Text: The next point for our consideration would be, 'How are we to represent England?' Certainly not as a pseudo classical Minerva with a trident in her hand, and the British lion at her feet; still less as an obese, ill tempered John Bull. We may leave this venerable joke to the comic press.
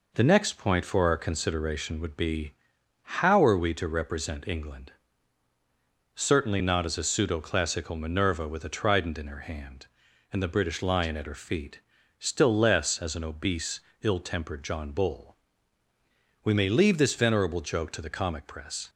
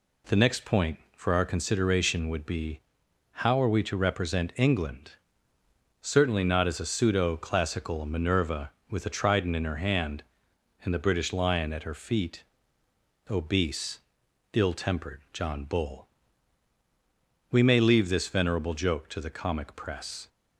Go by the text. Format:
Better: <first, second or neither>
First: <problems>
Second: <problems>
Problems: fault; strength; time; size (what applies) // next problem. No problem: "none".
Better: first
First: none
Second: skips "still less as an"; at 12.8 s